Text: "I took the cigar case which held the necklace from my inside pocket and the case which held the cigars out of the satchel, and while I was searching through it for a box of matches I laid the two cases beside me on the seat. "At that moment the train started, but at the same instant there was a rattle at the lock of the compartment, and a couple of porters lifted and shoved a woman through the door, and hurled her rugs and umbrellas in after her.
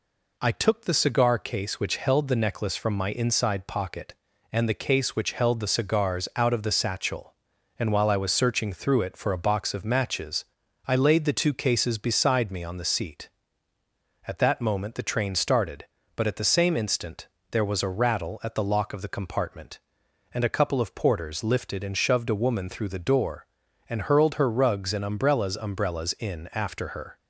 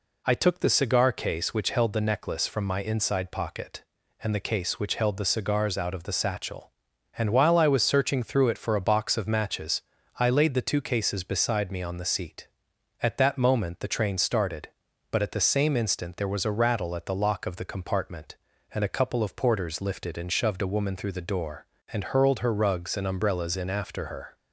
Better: second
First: pauses between "matches" and "I"; at 10.4 s; 0.40 s long // pauses between "instant" and "there"; slight; at 17.2 s; 0.22 s long // says "umbrellas" twice; at 25.5 s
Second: pauses between "matches" and "I"; at 9.7 s; 0.38 s long

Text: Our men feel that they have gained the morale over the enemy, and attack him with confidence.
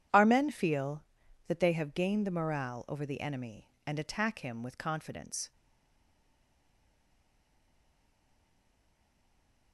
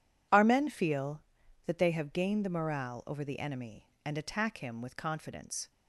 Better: second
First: stays silent after the last word; strong; from 5.5 s on; 4.2 s long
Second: none

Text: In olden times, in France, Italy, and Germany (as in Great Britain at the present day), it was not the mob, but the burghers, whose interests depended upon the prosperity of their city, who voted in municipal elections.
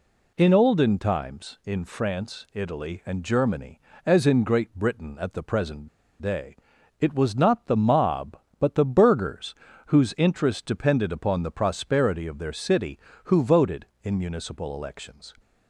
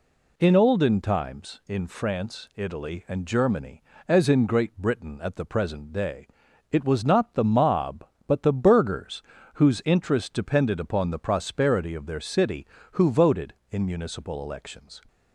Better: second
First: pauses between "present" and "day"; slight; at 5.8 s; 0.33 s long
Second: none

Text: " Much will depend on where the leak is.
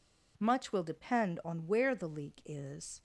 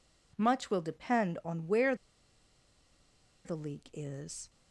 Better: first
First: none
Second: pauses between "where" and "the"; strong; at 1.9 s; 1.5 s long

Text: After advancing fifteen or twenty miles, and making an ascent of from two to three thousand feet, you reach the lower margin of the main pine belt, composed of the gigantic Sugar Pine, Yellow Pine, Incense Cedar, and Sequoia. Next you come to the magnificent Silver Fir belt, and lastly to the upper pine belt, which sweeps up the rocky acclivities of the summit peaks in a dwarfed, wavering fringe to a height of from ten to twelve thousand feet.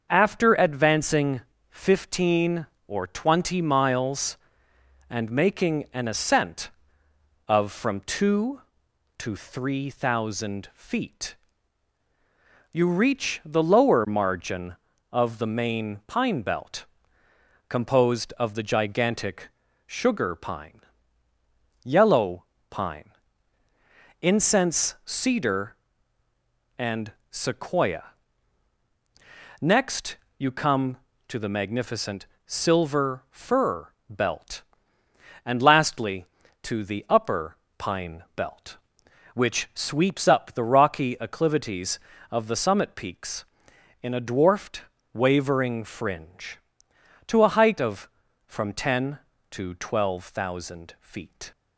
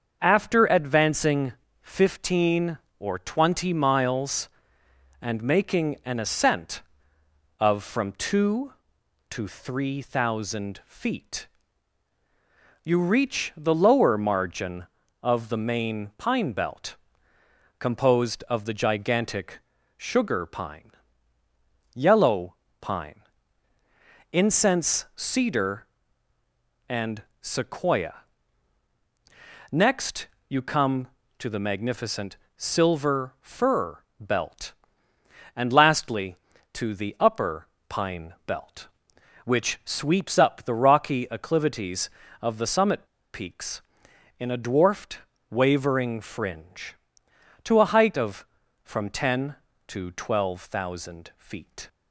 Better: first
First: starts louder than the rest; until 1.1 s; 6.5 dB // pauses between "advancing" and "fifteen"; slight; at 1.4 s; 0.28 s long // pauses between "gigantic" and "Sugar"; slight; at 19.4 s; 0.36 s long // pauses between "Yellow" and "Pine"; slight; at 22.4 s; 0.26 s long // pauses between "and" and "Sequoia"; slight; at 27.1 s; 0.18 s long // pauses between "Next" and "you"; slight; at 30.1 s; 0.22 s long // pauses between "magnificent" and "Silver"; slight; at 32.2 s; 0.20 s long // pauses between "Fir" and "belt"; slight; at 33.8 s; 0.22 s long // pauses between "upper" and "pine"; slight; at 37.5 s; 0.20 s long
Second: starts louder than the rest; until 1.2 s; 7 dB // pauses between "advancing" and "fifteen"; slight; at 1.5 s; 0.28 s long // pauses between "gigantic" and "Sugar"; slight; at 19.5 s; 0.36 s long // pauses between "Yellow" and "Pine"; slight; at 22.5 s; 0.26 s long // pauses between "and" and "Sequoia"; slight; at 27.2 s; 0.18 s long // pauses between "Next" and "you"; slight; at 30.2 s; 0.22 s long // pauses between "magnificent" and "Silver"; slight; at 32.3 s; 0.20 s long // pauses between "Fir" and "belt"; slight; at 33.9 s; 0.22 s long // pauses between "upper" and "pine"; slight; at 37.6 s; 0.20 s long // pauses between "summit" and "peaks"; slight; at 43.0 s; 0.27 s long

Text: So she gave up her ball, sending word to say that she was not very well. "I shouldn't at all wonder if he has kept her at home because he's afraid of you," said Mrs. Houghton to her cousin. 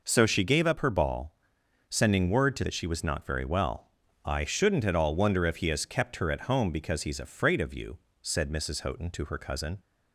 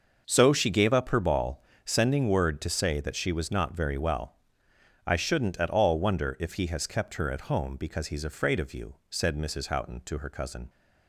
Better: second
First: skips "say"; at 2.6 s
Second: none

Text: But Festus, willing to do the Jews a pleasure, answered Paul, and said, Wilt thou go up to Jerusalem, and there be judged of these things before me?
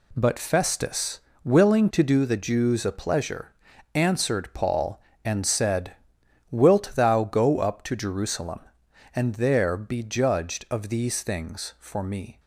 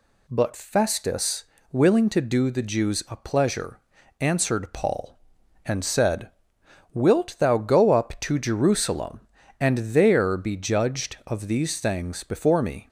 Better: second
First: says "for" for "before"; at 11.7 s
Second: none

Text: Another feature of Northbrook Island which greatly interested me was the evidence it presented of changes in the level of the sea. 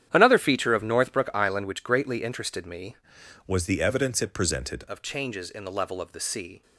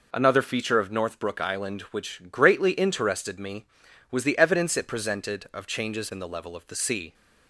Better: second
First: starts louder than the rest; strong; until 1.1 s; 10 dB // changes voice from "was" to "presented"; from 3.4 to 4.8 s; 1.4 s long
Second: none

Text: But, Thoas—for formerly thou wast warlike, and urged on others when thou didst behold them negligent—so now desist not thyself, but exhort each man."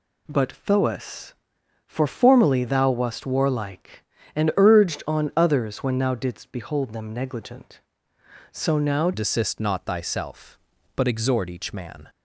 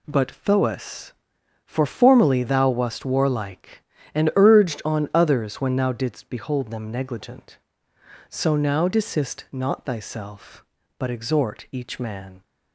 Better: second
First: changes voice at "desist"; from 9.1 s on; 2.9 s long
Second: none

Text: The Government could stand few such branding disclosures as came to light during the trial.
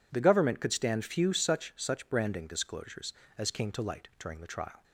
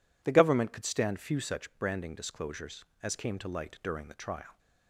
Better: second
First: says "such" twice; at 1.7 s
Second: none

